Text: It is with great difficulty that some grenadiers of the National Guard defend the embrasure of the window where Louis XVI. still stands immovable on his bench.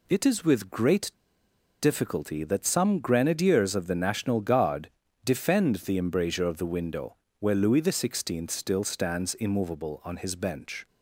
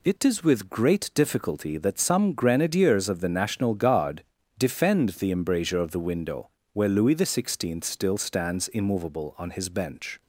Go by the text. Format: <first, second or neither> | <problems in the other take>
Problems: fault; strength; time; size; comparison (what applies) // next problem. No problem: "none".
second | pauses between "great" and "difficulty"; noticeable; at 1.0 s; 0.71 s long // pauses between "Guard" and "defend"; slight; at 4.8 s; 0.36 s long; slight in the second // pauses between "window" and "where"; slight; at 7.1 s; 0.24 s long; slight in the second